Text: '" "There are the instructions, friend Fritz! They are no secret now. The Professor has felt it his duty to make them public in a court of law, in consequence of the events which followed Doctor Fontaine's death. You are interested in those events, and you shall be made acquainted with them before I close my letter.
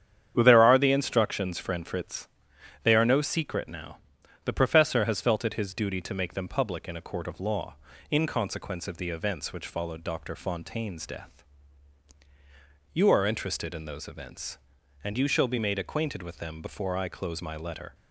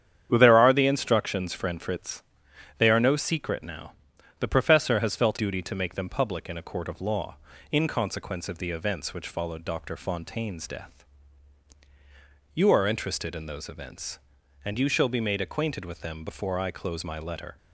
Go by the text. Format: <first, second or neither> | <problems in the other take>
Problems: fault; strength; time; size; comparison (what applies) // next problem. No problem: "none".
first | starts louder than the rest; strong; until 1.3 s; 9 dB; strong in the first // skips "it his"; at 5.3 s